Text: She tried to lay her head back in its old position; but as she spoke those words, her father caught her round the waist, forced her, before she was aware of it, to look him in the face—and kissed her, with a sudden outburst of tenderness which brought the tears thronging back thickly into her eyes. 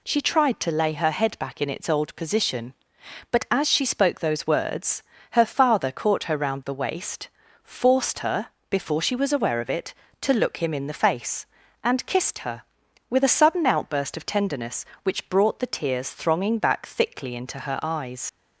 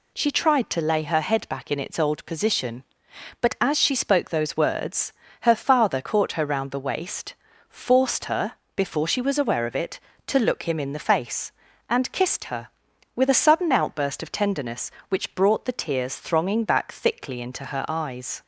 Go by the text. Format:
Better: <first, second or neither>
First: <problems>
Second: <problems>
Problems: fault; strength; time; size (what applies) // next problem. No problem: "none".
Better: second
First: leaves "eyes" unfinished; at 18.2 s; 65 ms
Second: none